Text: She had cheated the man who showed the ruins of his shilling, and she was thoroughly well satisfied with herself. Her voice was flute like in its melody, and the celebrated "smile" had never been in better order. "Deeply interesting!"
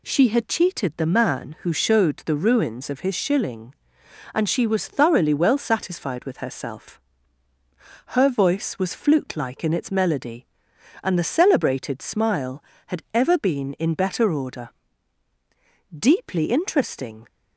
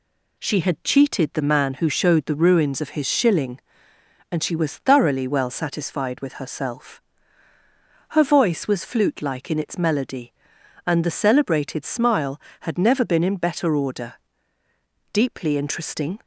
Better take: second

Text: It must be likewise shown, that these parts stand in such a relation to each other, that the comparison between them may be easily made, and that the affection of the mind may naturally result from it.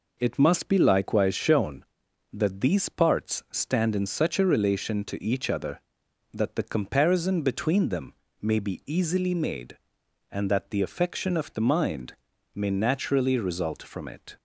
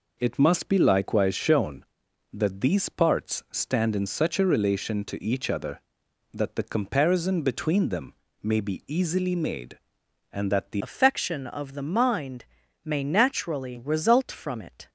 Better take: first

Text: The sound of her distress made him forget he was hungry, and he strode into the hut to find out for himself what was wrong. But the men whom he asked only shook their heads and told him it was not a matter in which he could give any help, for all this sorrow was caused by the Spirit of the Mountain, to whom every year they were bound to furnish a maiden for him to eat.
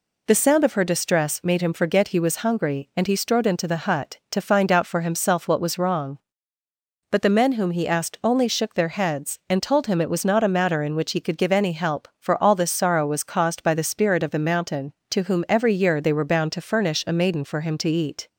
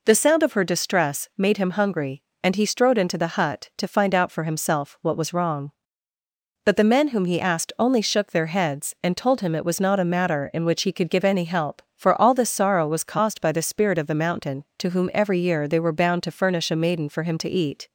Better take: first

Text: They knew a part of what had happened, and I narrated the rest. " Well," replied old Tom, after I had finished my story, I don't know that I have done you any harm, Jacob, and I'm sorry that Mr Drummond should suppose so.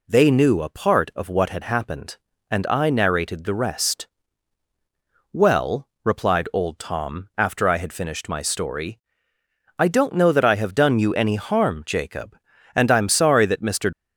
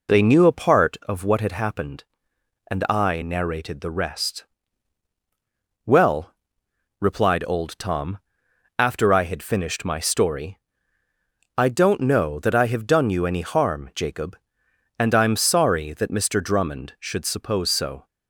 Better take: second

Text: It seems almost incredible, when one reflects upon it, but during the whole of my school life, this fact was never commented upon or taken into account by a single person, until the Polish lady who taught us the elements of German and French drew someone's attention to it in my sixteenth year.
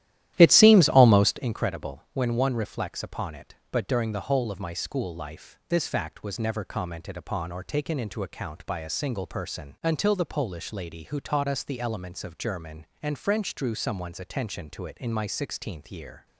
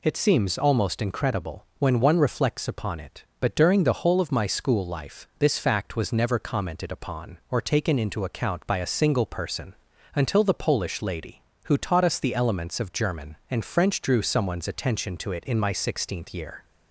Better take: second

